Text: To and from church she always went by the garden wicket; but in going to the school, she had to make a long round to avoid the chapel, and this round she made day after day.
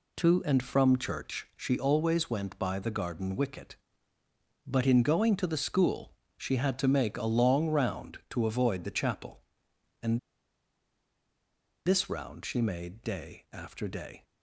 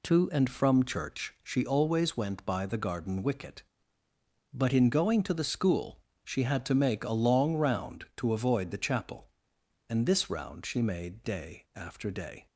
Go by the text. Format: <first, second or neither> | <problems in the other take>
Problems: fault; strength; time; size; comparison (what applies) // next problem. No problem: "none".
second | pauses between "and" and "this"; strong; at 10.1 s; 1.6 s long